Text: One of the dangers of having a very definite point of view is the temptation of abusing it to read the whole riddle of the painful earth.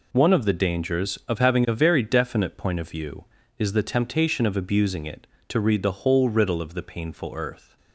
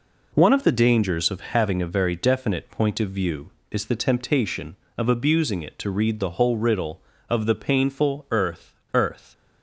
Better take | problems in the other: first | says "earth" twice; at 8.9 s

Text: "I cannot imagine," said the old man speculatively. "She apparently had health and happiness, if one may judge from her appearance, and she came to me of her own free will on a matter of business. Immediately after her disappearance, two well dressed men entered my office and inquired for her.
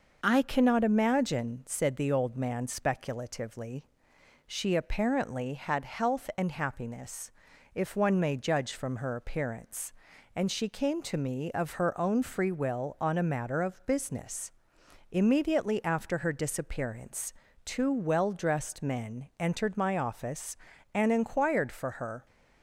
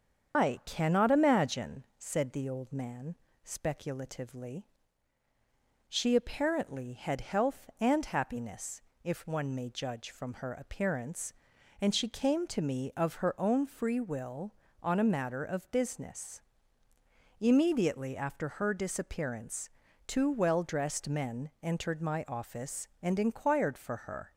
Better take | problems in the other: first | loses the start of "I"; at 0.3 s; 160 ms // starts louder than the rest; strong; until 1.4 s; 7.5 dB // pauses between "man" and "speculatively"; slight; at 3.1 s; 0.28 s long

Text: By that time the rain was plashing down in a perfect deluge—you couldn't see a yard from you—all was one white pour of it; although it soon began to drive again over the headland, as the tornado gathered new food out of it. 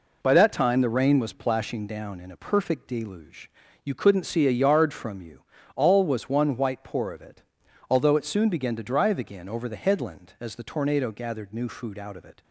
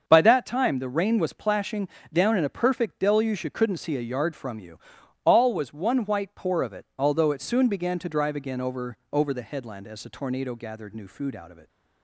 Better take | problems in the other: first | starts louder than the rest; until 1.0 s; 6.5 dB // pauses between "plashing" and "down"; slight; at 1.8 s; 0.24 s long // says "over" twice; at 9.1 s

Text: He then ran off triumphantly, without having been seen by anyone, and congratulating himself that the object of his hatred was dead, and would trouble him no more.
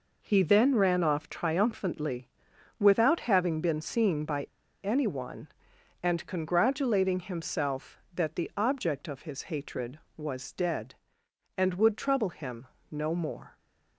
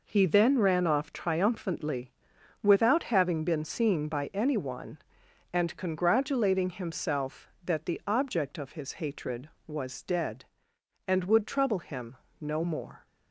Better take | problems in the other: second | pauses between "by" and "anyone"; at 4.4 s; 0.37 s long // pauses between "him" and "no"; slight; at 12.6 s; 0.22 s long; slight in the second

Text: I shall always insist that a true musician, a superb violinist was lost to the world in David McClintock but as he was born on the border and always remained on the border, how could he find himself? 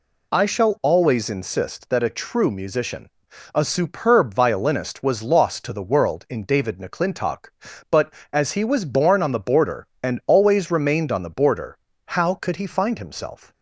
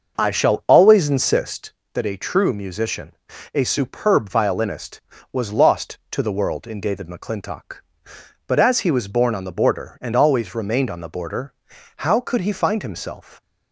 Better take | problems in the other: first | starts louder than the rest; until 1.9 s; 6 dB

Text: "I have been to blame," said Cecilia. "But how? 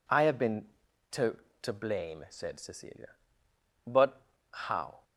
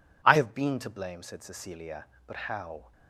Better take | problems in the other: second | says "to" twice; at 1.6 s // pauses between "But" and "how"; slight; at 4.2 s; 0.30 s long

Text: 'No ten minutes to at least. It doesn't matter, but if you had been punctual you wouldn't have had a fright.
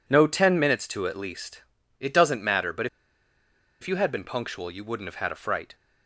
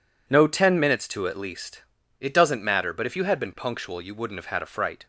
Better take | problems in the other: second | pauses between "but" and "if"; noticeable; at 2.8 s; 0.94 s long

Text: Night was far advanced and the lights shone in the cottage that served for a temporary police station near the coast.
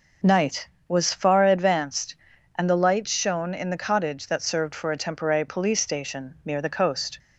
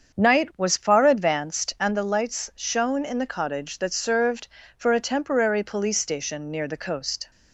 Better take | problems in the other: first | starts louder than the rest; until 1.9 s; 7 dB

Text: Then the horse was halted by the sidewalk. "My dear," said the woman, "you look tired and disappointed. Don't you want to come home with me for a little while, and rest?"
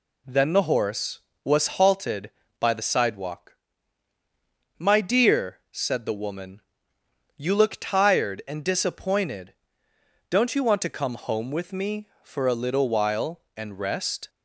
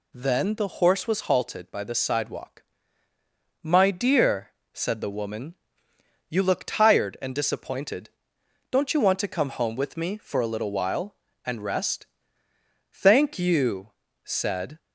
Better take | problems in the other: first | goes on to say "Thank you said"; strong; from 12.9 s on; 1.8 s long

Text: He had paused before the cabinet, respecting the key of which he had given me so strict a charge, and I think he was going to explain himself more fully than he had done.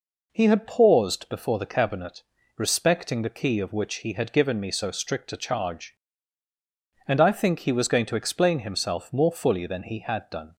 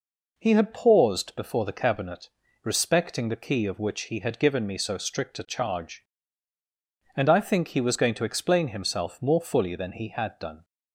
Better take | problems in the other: neither | none

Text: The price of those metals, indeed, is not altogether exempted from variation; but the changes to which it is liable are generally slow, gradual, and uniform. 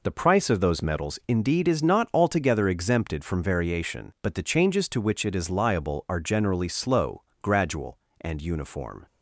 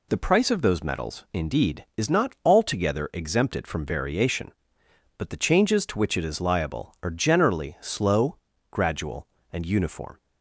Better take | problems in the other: neither | none

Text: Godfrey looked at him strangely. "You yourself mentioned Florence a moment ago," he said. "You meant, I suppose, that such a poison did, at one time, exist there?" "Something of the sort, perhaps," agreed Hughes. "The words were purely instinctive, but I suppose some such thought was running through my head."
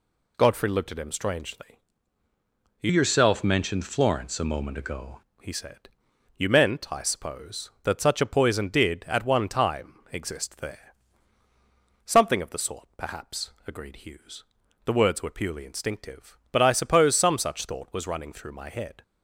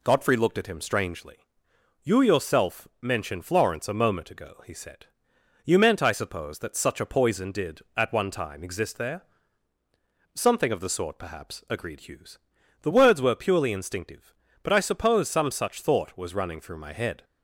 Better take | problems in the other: second | changes voice from "yourself" to "ago"; from 2.8 to 5.2 s; 2.4 s long

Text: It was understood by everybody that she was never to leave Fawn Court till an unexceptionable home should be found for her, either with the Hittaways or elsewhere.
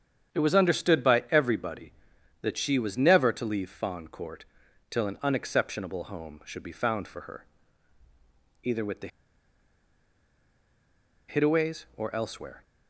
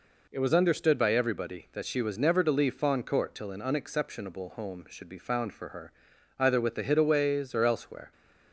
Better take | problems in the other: second | starts louder than the rest; strong; until 1.3 s; 8.5 dB // pauses between "Court" and "till"; at 4.4 s; 0.44 s long // pauses between "the" and "Hittaways"; strong; at 9.0 s; 2.2 s long

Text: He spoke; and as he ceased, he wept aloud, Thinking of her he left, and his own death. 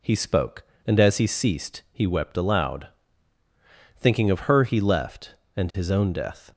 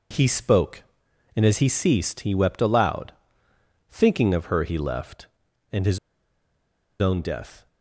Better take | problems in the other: first | pauses between "his" and "own"; at 5.9 s; 1.0 s long

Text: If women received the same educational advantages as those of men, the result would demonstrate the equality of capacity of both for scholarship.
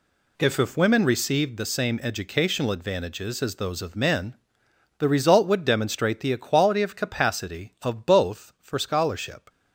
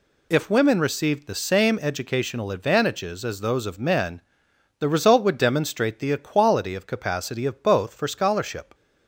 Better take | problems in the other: second | says "If" twice; at 0.5 s

